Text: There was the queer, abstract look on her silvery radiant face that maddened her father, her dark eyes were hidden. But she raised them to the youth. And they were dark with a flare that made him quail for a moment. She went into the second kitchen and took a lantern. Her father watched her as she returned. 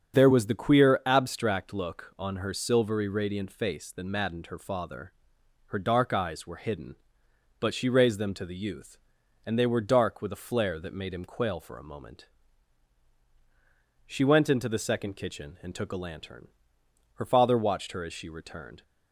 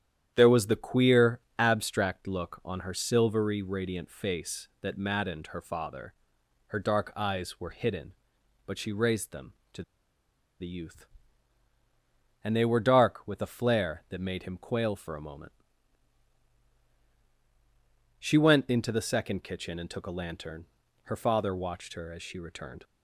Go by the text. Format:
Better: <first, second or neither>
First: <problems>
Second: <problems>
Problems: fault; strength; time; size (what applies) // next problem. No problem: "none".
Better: first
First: starts louder than the rest; strong; until 1.2 s; 7 dB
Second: starts louder than the rest; strong; until 1.3 s; 10 dB // pauses between "to" and "the"; noticeable; at 9.8 s; 0.78 s long